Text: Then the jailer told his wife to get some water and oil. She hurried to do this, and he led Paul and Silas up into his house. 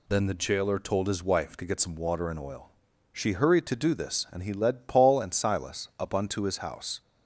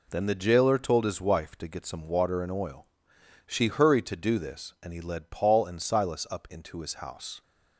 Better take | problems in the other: second | says "unto" for "into"; at 6.1 s

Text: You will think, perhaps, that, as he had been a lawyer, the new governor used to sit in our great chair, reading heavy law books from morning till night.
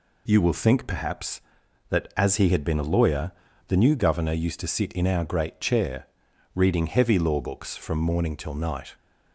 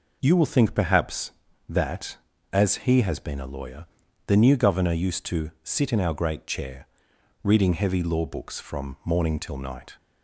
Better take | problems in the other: first | says "has" for "had"; at 3.0 s

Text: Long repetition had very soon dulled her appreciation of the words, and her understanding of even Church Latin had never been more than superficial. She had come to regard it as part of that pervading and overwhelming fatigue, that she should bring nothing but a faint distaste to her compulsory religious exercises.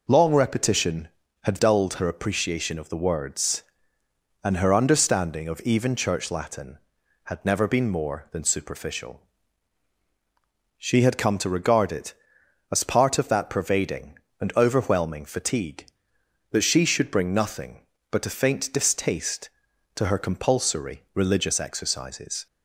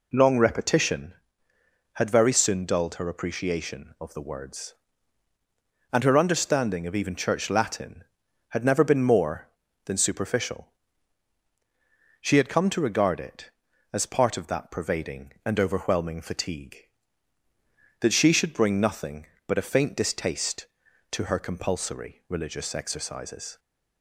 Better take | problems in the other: second | skips "very soon"; at 1.5 s

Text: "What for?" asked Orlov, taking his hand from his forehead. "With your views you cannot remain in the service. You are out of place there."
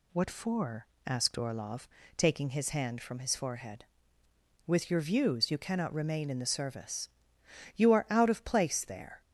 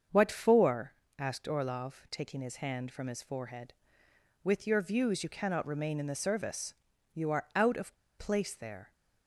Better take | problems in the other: first | starts louder than the rest; until 1.3 s; 7 dB // pauses between "of" and "place"; slight; at 7.9 s; 0.23 s long

